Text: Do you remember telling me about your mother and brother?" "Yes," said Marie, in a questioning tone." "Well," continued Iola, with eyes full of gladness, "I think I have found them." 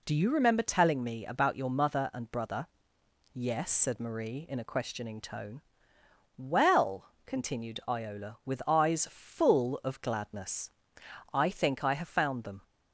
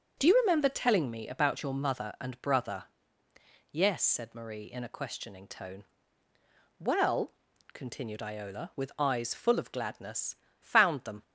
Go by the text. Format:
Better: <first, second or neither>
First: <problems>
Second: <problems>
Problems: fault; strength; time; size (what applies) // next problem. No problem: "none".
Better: first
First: none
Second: skips "I think I have"; at 10.4 s